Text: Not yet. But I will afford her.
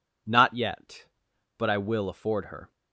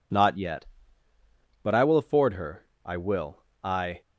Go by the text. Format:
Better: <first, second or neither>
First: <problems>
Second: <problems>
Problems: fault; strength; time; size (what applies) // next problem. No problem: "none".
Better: first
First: none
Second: goes on to say "I will I"; noticeable; from 2.8 s on; 1.1 s long